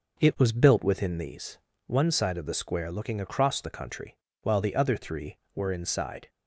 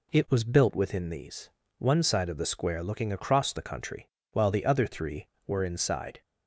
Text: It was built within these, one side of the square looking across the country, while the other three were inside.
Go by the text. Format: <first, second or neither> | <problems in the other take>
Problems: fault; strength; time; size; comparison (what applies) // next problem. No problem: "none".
second | starts louder than the rest; noticeable; until 1.8 s; 5 dB